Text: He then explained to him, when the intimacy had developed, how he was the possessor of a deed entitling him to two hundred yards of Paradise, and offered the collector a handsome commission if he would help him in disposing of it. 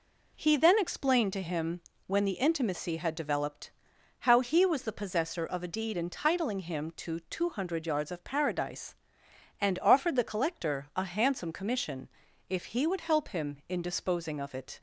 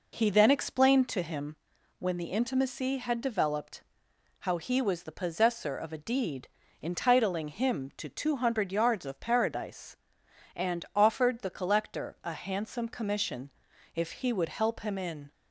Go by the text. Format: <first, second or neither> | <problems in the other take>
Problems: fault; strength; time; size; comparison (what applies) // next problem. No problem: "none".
first | pauses between "deed" and "entitling"; slight; at 6.4 s; 0.34 s long // pauses between "commission" and "if"; noticeable; at 13.4 s; 0.46 s long; also in the first // stops before "disposing of it"; at 15.3 s